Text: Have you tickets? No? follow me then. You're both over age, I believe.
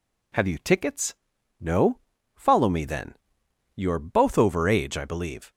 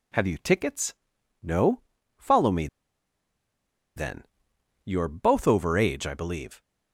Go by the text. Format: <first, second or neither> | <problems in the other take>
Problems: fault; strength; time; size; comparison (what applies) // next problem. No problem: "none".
first | pauses between "me" and "then"; strong; at 2.6 s; 1.2 s long